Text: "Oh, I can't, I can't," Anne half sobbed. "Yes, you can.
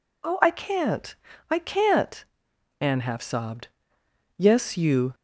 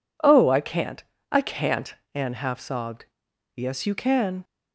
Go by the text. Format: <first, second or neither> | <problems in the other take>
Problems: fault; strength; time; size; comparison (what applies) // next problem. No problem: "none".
second | stops before "can"; at 5.1 s